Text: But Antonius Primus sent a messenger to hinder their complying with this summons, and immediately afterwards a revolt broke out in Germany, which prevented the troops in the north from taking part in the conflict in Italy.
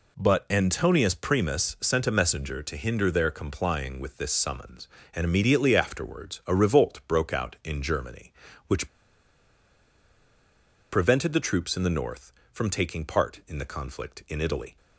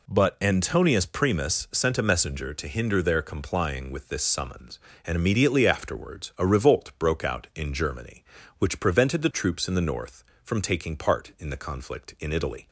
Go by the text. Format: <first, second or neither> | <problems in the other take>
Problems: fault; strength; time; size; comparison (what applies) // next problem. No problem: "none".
second | pauses between "which" and "prevented"; strong; at 8.8 s; 2.0 s long